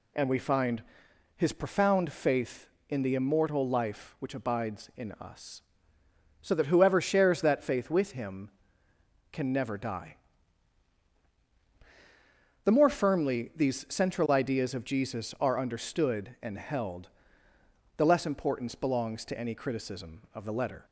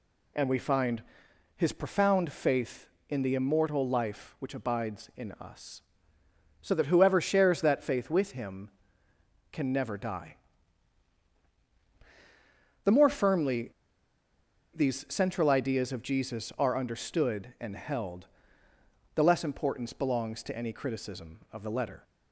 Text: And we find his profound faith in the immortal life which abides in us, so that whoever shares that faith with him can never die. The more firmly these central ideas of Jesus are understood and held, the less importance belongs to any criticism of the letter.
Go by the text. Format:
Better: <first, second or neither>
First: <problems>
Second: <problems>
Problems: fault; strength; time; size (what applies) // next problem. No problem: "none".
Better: first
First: pauses between "find" and "his"; noticeable; at 0.8 s; 0.54 s long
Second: pauses between "find" and "his"; noticeable; at 1.0 s; 0.54 s long // pauses between "firmly" and "these"; at 13.6 s; 1.0 s long